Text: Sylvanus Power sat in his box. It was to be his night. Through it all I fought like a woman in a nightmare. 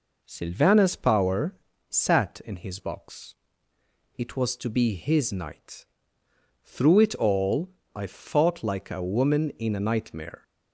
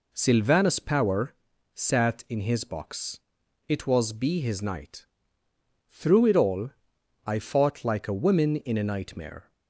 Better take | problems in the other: first | pauses between "Power" and "sat"; at 1.3 s; 0.40 s long; slight in the first // skips "to"; at 4.1 s // pauses between "all" and "I"; noticeable; at 6.6 s; 0.56 s long; slight in the first

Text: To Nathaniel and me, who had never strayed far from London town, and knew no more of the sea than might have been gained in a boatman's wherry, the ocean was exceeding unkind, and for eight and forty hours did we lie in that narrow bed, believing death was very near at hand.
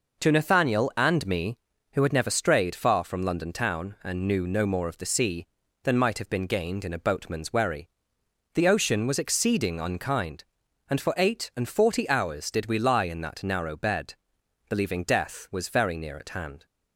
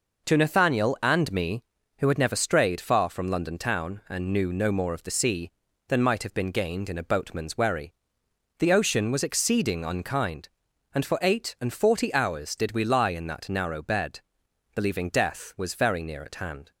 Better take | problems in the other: neither | none

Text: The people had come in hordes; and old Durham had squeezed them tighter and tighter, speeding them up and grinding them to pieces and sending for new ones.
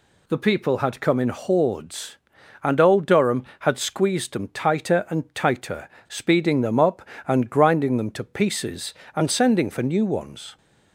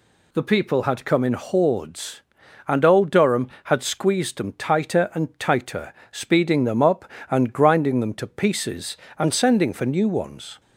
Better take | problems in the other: neither | none

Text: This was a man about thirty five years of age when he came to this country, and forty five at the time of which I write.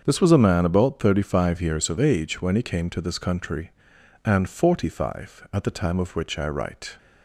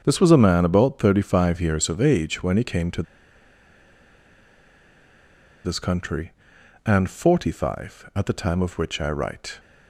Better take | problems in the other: first | starts louder than the rest; until 1.0 s; 7 dB; also in the first // pauses between "to" and "this"; strong; at 3.0 s; 2.6 s long

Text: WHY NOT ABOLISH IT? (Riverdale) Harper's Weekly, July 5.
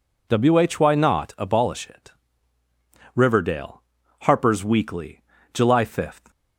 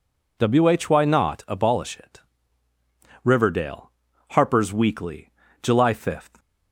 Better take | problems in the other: neither | none

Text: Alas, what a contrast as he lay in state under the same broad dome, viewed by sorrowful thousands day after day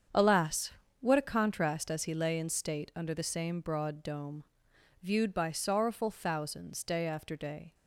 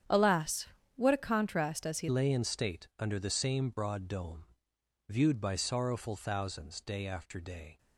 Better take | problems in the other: first | starts louder than the rest; strong; until 1.4 s; 9 dB; strong in the first // changes voice at "lay"; from 2.0 s on; 5.7 s long

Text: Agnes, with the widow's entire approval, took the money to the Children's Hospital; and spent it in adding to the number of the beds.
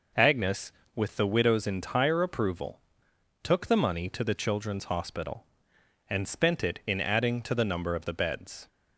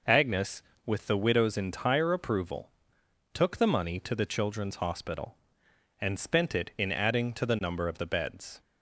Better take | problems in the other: neither | none

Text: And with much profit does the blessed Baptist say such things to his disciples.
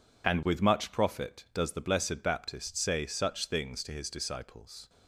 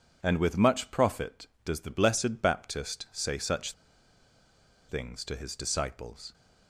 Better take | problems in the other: first | pauses between "such" and "things"; at 3.7 s; 1.1 s long

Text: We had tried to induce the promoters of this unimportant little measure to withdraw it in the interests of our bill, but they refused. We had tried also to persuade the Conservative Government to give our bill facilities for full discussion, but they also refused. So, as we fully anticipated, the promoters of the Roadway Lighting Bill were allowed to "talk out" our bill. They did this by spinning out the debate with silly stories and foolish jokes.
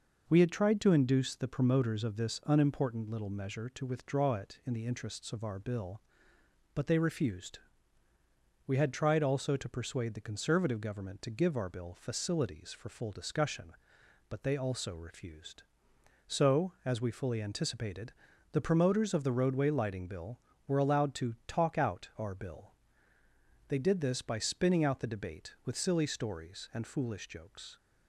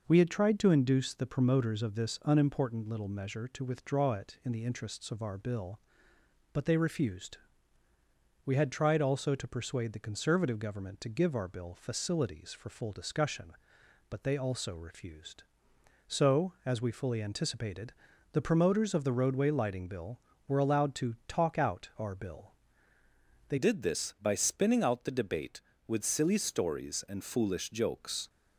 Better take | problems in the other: first | changes voice at "did"; from 23.5 s on; 4.7 s long

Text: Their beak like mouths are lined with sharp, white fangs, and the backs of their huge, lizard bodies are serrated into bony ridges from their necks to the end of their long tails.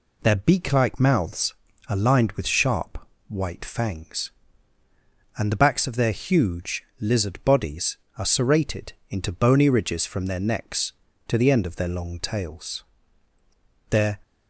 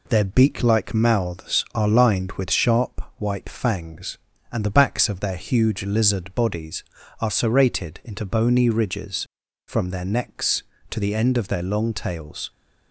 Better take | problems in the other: second | pauses between "serrated" and "into"; slight; at 8.9 s; 0.18 s long // goes on to say "Their"; slight; from 13.9 s on; 0.28 s long

